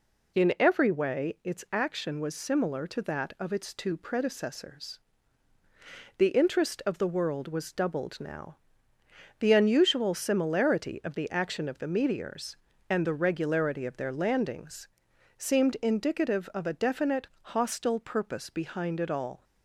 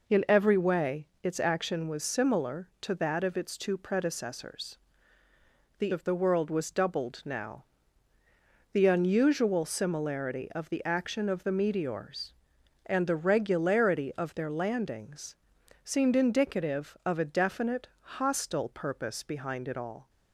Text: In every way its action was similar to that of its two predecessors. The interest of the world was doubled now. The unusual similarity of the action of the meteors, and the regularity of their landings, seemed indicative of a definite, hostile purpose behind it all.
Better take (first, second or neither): first